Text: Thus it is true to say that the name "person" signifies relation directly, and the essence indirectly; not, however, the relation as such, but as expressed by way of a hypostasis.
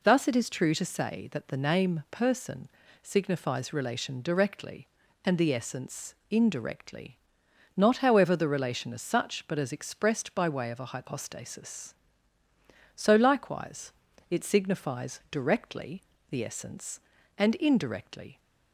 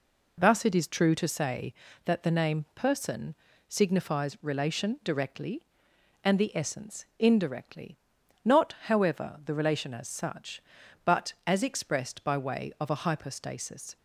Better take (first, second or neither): second